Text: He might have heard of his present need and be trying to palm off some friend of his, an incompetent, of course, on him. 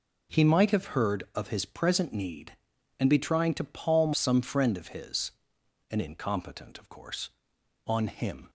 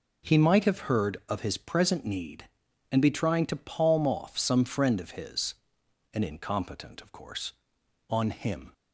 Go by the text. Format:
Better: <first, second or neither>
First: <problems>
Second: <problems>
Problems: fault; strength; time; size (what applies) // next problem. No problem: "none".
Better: second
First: skips "off"; at 4.1 s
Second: none